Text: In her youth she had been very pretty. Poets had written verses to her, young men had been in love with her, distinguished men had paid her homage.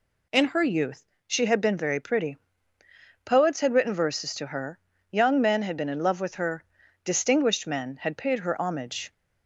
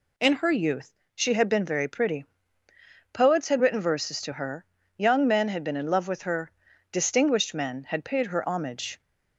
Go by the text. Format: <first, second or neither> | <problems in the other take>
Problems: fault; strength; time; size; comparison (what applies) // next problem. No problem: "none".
neither | pauses between "youth" and "she"; slight; the same in both